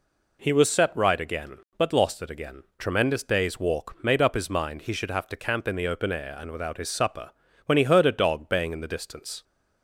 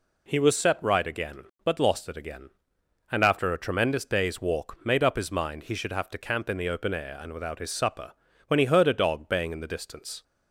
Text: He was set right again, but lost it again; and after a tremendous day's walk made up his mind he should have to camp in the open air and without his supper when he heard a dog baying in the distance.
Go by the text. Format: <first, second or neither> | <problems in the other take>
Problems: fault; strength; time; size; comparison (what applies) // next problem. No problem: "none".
second | skips "and after a"; at 2.7 s // pauses between "supper" and "when"; at 7.2 s; 0.38 s long; also in the second